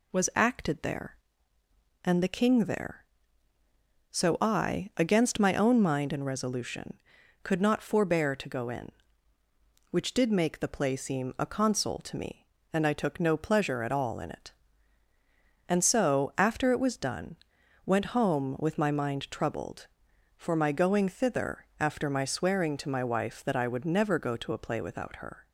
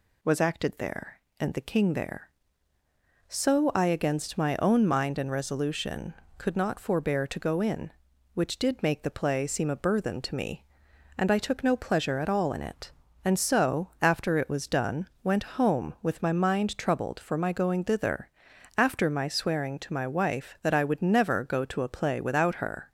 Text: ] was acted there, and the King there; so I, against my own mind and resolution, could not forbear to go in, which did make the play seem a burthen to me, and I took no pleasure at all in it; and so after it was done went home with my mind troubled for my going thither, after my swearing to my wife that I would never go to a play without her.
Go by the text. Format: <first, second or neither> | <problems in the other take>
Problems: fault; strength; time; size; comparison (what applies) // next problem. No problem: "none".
second | says "console" for "burthen"; at 11.4 s // pauses between "done" and "went"; noticeable; at 17.3 s; 0.48 s long; slight in the second